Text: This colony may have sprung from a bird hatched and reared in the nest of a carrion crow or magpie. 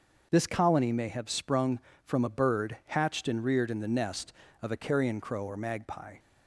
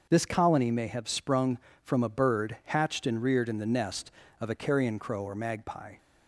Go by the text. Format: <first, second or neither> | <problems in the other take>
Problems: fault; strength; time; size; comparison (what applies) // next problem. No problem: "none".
neither | starts louder than the rest; the same in both